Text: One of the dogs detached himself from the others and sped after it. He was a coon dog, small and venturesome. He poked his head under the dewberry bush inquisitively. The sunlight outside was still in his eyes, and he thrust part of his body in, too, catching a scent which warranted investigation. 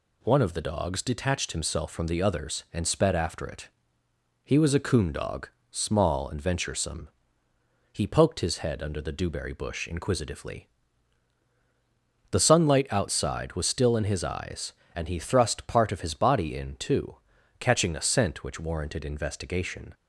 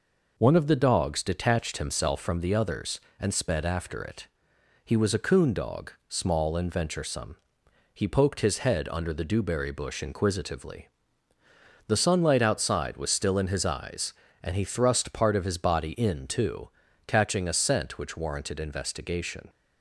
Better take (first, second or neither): neither